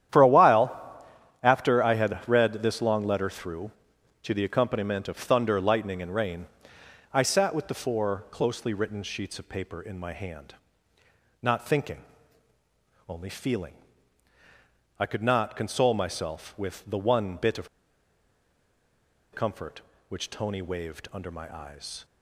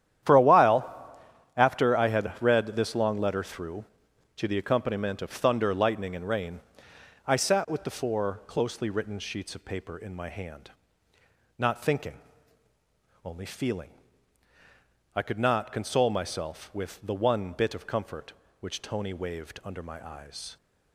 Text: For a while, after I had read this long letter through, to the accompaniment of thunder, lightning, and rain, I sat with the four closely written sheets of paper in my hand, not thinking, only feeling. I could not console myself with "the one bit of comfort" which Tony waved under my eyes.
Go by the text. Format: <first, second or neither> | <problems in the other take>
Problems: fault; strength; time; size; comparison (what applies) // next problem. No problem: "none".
second | starts louder than the rest; strong; until 1.7 s; 10.5 dB; strong in the second // pauses between "of" and "comfort"; strong; at 17.6 s; 1.6 s long